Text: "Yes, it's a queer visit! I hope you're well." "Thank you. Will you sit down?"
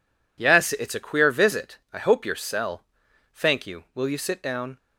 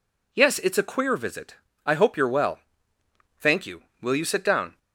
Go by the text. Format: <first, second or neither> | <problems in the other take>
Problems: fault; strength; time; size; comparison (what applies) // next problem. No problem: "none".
second | says "cell" for "well"; at 2.3 s